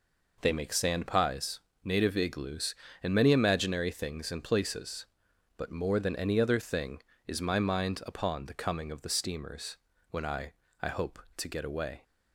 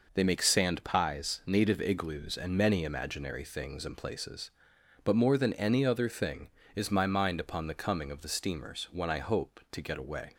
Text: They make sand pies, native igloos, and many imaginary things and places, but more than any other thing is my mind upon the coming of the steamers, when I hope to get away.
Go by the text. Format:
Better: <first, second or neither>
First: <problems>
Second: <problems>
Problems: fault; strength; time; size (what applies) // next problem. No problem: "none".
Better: second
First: says "I" twice; at 10.8 s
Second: none